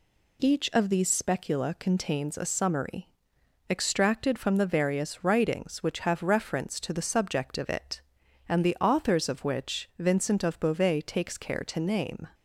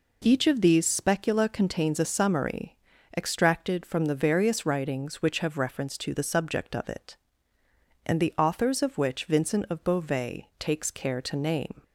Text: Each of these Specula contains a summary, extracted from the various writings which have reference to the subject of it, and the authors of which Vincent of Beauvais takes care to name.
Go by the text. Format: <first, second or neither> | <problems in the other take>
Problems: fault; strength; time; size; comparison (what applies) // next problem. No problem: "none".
neither | none